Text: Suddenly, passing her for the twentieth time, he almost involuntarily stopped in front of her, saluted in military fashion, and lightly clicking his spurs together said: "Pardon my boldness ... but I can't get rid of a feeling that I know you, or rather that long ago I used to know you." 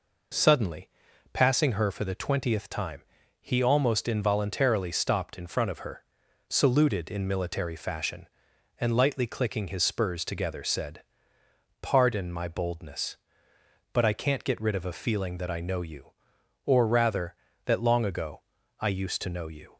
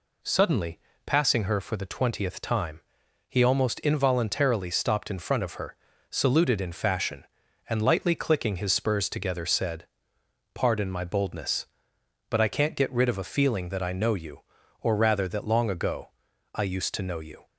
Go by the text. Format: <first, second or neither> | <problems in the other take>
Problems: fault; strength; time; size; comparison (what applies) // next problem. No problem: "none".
first | skips "military"; at 6.7 s // pauses between "ago" and "I"; at 16.1 s; 0.44 s long; also in the first